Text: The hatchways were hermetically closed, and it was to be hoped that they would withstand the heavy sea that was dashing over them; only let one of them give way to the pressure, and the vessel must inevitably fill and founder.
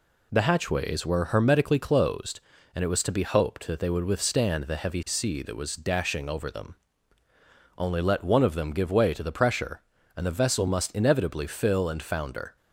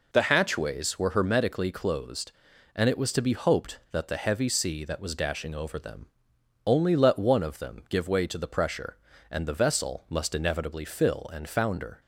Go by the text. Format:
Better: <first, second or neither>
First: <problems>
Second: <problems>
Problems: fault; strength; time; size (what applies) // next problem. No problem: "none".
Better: first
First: none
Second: skips "they would withstand"; at 4.0 s